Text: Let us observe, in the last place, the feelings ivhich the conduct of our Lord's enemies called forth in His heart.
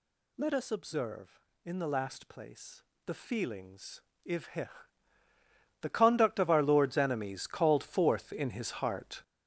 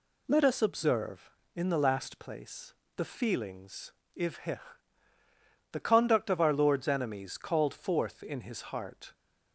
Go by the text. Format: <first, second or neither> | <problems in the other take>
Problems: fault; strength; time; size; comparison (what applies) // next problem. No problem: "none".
second | gets louder; strong; throughout; 8 dB // pauses between "feelings" and "ivhich"; slight; at 4.0 s; 0.28 s long; slight in the second // pauses between "ivhich" and "the"; at 4.6 s; 1.1 s long; also in the second